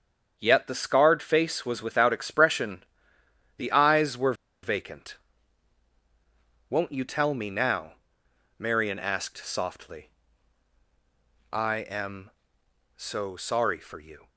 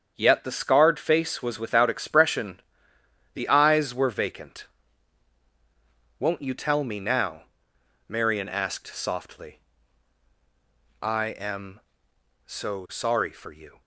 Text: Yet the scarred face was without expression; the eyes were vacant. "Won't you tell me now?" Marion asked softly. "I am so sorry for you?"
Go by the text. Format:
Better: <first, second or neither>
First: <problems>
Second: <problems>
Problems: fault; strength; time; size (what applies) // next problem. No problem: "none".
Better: second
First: starts louder than the rest; strong; until 1.4 s; 7.5 dB // pauses between "were" and "vacant"; slight; at 4.3 s; 0.29 s long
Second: starts louder than the rest; strong; until 1.1 s; 7.5 dB